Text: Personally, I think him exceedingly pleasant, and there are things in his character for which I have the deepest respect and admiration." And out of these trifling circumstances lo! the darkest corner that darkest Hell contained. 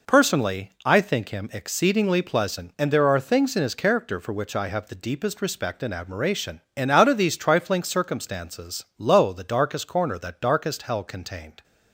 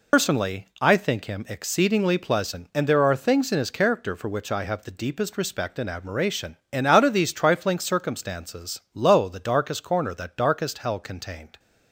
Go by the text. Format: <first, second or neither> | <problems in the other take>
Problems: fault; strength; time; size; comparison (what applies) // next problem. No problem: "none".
first | loses the start of "Personally"; at 0.1 s; 100 ms